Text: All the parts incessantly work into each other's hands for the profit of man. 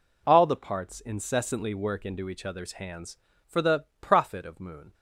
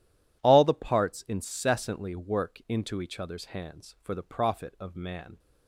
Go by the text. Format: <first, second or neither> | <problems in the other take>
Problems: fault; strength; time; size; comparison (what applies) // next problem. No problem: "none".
second | pauses between "the" and "profit"; slight; at 3.8 s; 0.16 s long // says "moon" for "man"; at 4.5 s